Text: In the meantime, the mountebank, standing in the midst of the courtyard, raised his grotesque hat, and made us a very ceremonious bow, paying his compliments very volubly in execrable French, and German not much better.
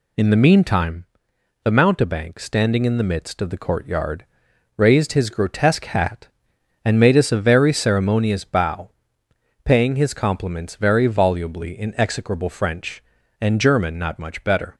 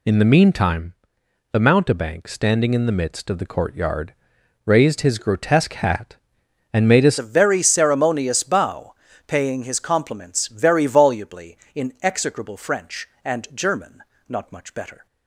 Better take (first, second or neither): first